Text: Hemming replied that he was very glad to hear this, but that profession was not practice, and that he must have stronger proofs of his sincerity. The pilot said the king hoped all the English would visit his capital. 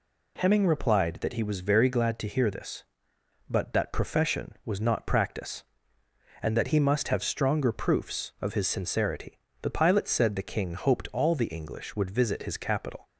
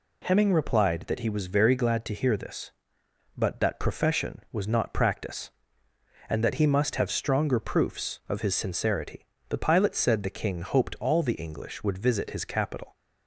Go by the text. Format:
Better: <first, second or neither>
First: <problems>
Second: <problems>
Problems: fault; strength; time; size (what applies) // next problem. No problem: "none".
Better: neither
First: none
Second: none